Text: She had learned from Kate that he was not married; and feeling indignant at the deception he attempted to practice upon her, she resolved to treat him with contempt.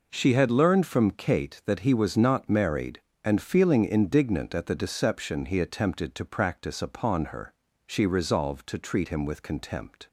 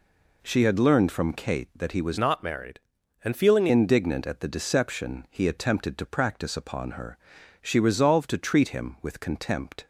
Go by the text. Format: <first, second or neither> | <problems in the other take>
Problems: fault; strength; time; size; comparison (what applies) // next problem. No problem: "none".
first | changes voice from "not" to "feeling"; from 2.1 to 3.6 s; 1.5 s long